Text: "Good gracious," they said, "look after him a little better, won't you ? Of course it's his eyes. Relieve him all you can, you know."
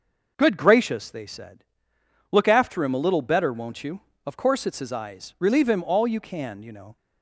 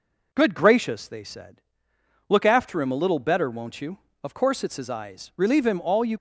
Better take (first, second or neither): first